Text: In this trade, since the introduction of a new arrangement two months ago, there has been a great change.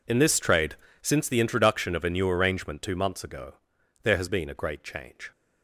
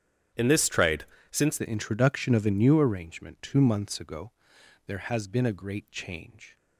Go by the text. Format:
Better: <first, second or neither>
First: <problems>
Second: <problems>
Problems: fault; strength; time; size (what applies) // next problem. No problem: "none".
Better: first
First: none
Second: starts louder than the rest; strong; until 1.6 s; 9 dB // changes voice at "the"; from 1.5 s on; 5.0 s long